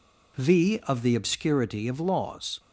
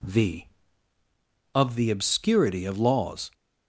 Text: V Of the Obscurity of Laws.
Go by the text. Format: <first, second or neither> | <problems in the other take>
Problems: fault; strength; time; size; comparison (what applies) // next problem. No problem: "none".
neither | none